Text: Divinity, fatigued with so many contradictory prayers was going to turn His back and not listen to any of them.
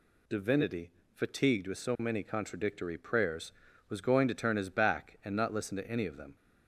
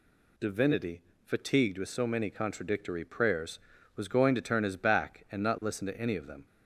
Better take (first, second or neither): neither